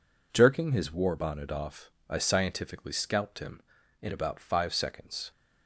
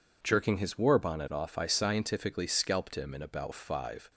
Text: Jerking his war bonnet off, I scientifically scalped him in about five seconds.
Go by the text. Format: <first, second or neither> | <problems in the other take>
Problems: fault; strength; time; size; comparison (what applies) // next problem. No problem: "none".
first | stops before "seconds"; at 4.1 s